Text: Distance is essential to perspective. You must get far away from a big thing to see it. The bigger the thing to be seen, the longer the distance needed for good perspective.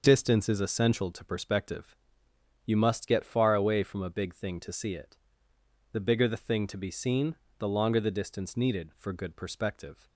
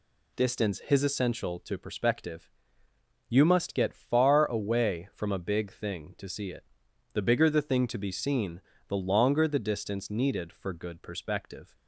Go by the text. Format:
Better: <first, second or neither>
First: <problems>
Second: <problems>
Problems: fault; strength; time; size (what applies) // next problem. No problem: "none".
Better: first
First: none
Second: says "his" for "is"; at 0.8 s